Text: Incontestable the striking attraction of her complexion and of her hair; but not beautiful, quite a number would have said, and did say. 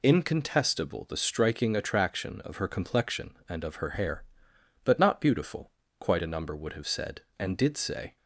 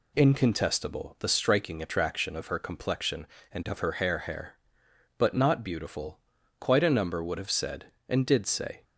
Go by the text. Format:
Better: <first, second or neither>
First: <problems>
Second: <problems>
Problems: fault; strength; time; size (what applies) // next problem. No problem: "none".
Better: first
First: none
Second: says "hair" twice; at 4.1 s